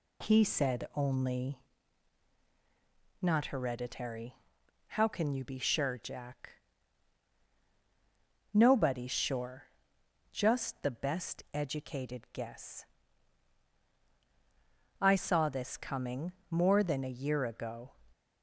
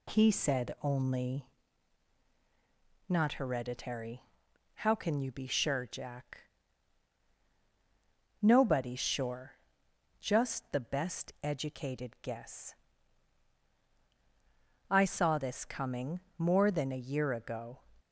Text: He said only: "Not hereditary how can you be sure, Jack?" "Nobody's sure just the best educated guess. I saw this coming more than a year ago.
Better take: neither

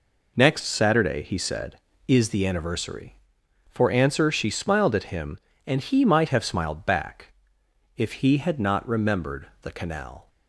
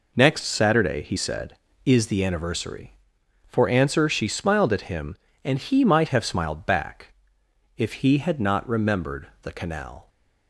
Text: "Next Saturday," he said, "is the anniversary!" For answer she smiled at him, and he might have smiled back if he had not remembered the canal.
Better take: neither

